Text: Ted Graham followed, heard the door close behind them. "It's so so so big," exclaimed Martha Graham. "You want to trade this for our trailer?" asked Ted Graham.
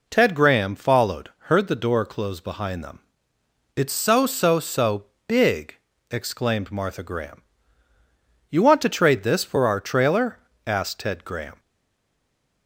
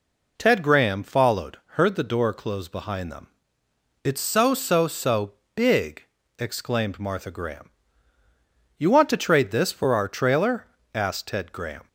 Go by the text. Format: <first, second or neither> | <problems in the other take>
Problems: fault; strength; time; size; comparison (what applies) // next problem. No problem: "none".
second | pauses between "so" and "big"; slight; at 5.0 s; 0.24 s long; slight in the second // stays silent after the last word; from 11.5 s on; 1.1 s long